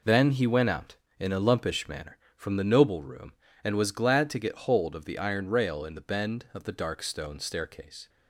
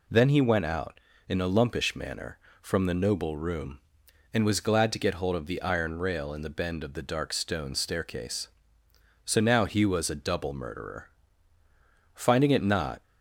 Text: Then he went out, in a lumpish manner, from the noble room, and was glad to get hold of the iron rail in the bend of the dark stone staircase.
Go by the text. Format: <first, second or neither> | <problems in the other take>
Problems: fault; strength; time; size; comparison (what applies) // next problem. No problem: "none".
first | goes on to say "So now he was a double murderer Finding it not"; strong; from 9.2 s on; 3.7 s long